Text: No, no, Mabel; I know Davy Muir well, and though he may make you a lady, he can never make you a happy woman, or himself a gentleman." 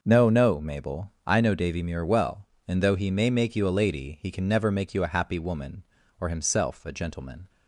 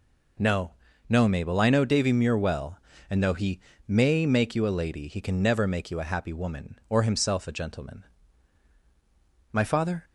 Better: first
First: none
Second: pauses between "he" and "may"; slight; at 3.5 s; 0.30 s long // goes on to say "My father"; from 9.5 s on; 0.52 s long

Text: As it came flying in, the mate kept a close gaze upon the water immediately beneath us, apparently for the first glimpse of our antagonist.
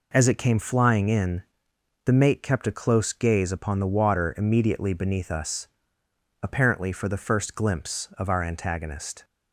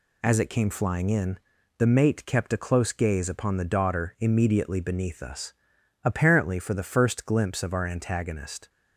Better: first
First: none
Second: says "daughter" for "water"; at 3.6 s

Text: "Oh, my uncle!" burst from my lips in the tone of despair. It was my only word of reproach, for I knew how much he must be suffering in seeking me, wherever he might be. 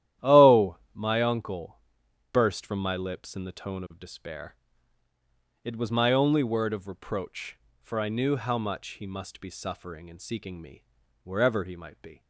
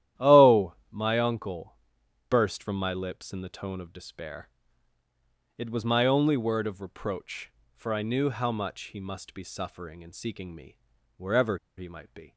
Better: first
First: starts louder than the rest; strong; until 1.3 s; 12 dB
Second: starts louder than the rest; strong; until 1.3 s; 12 dB // pauses between "wherever" and "he"; slight; at 11.5 s; 0.19 s long

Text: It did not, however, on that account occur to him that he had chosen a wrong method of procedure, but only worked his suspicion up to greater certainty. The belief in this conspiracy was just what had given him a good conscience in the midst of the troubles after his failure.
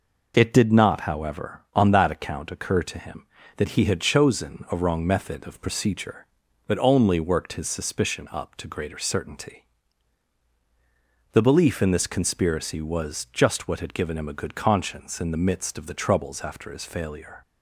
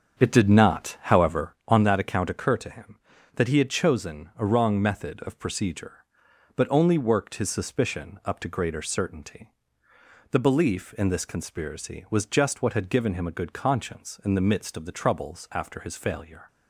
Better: first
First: none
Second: starts louder than the rest; strong; until 1.9 s; 7.5 dB

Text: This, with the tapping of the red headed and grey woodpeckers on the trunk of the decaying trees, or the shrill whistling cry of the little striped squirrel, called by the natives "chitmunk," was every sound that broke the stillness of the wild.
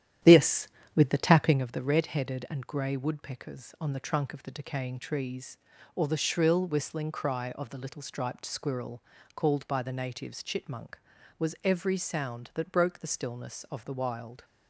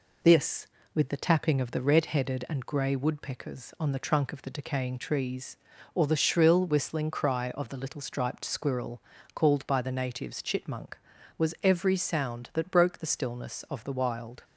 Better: second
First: starts louder than the rest; strong; until 1.6 s; 11 dB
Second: none

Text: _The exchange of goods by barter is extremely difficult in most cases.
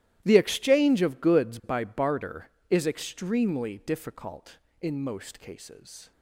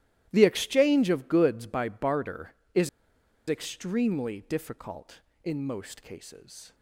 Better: first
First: starts louder than the rest; strong; until 1.2 s; 14 dB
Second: starts louder than the rest; strong; until 1.3 s; 14 dB // pauses between "is" and "extremely"; noticeable; at 2.8 s; 0.61 s long

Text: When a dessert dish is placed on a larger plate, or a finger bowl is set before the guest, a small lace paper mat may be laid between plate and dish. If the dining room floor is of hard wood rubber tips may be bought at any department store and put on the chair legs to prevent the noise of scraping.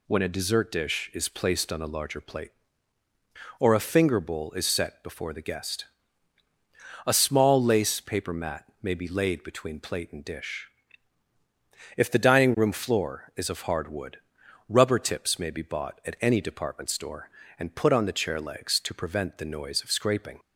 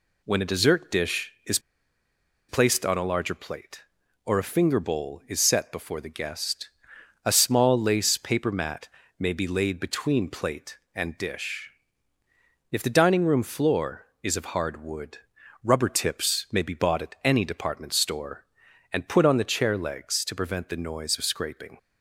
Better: first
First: pauses between "mat" and "may"; slight; at 8.6 s; 0.18 s long // pauses between "wood" and "rubber"; noticeable; at 14.1 s; 0.50 s long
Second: pauses between "is" and "placed"; noticeable; at 1.5 s; 0.90 s long // pauses between "mat" and "may"; slight; at 8.8 s; 0.28 s long // pauses between "wood" and "rubber"; noticeable; at 15.1 s; 0.46 s long

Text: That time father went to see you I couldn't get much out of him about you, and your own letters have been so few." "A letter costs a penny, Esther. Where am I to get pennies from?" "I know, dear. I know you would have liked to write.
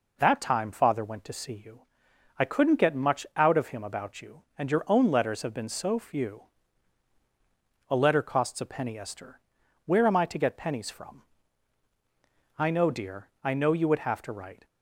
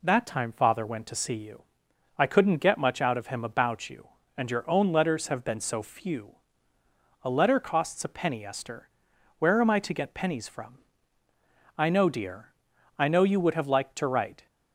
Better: second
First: pauses between "you" and "I"; noticeable; at 1.8 s; 0.54 s long // skips "liked"; at 14.2 s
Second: pauses between "you" and "I"; noticeable; at 1.6 s; 0.54 s long

